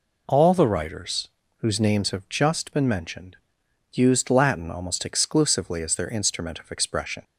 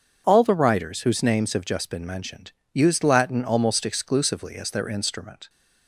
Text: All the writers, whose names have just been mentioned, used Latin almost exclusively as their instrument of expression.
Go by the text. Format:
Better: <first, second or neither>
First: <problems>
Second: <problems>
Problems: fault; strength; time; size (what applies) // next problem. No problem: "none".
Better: first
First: none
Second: starts louder than the rest; until 1.2 s; 7 dB // stops before "of expression"; at 5.4 s